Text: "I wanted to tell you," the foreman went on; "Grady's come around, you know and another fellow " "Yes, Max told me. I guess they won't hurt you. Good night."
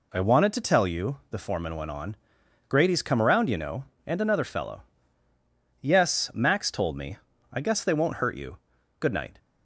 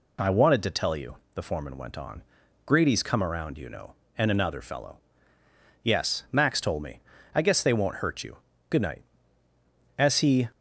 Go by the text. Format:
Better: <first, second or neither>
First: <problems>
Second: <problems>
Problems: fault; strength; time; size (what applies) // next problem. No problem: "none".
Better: first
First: none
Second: goes on to say "As he"; from 9.9 s on; 0.52 s long